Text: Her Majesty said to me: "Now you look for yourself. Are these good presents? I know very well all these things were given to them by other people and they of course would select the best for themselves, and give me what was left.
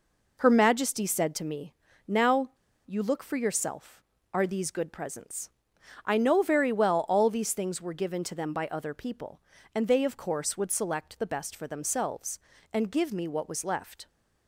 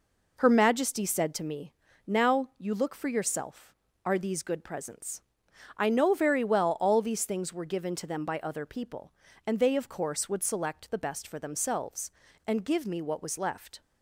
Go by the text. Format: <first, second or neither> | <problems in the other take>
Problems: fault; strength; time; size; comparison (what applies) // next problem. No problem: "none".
second | pauses between "Now" and "you"; slight; at 2.5 s; 0.35 s long